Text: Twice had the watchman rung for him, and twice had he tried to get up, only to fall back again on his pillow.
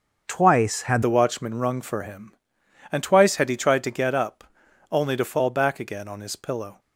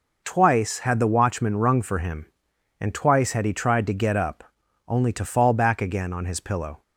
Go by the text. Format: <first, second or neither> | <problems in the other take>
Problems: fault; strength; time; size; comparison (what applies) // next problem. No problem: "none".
second | starts louder than the rest; until 1.2 s; 6 dB // changes voice at "the"; from 1.0 s on; 5.7 s long